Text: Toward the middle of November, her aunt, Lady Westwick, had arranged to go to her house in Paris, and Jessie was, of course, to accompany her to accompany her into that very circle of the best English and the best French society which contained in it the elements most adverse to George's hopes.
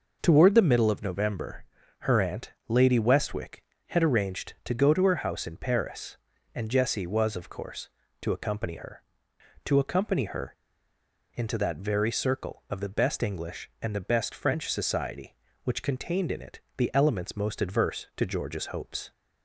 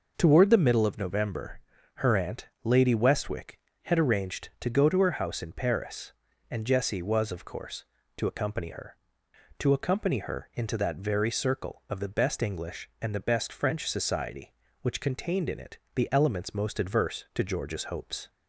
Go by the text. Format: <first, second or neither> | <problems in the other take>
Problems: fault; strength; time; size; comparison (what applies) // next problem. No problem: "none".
second | pauses between "her" and "into"; noticeable; at 10.5 s; 0.80 s long // pauses between "it" and "the"; slight; at 16.5 s; 0.16 s long; slight in the second